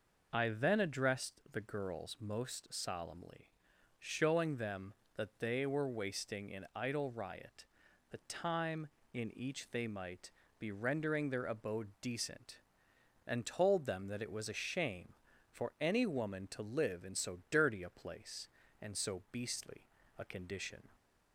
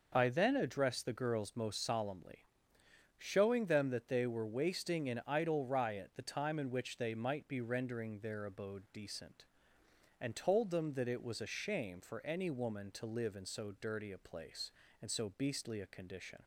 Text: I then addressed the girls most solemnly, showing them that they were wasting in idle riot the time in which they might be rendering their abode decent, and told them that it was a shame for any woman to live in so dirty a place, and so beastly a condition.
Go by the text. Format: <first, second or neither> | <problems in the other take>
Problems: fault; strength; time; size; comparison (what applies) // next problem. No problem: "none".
second | pauses between "riot" and "the"; noticeable; at 7.6 s; 0.46 s long // says "each" for "which"; at 9.3 s // pauses between "might" and "be"; slight; at 10.3 s; 0.28 s long // pauses between "beastly" and "a"; at 19.8 s; 0.38 s long